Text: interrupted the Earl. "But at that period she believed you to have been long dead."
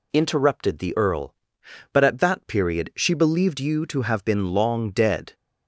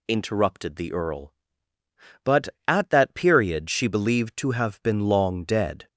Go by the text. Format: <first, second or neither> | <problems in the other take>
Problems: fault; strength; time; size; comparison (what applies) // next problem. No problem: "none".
first | skips "you"; at 4.3 s